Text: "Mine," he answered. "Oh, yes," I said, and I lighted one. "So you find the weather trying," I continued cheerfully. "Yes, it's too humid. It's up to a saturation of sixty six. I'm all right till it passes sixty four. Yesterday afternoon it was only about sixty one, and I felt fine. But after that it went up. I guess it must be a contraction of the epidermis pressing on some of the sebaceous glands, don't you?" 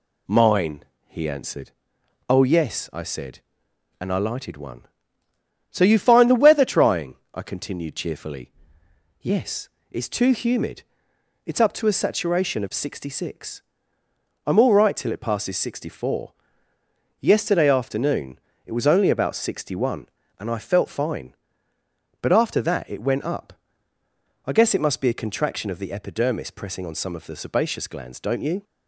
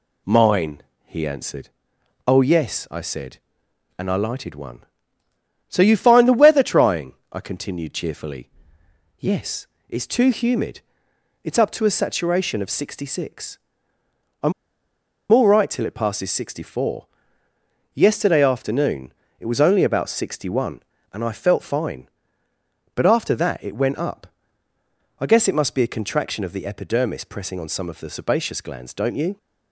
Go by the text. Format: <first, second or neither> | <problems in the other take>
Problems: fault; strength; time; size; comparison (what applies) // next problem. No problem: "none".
first | pauses between "I'm" and "all"; noticeable; at 14.5 s; 0.80 s long // pauses between "afternoon" and "it"; slight; at 19.1 s; 0.26 s long; slight in the first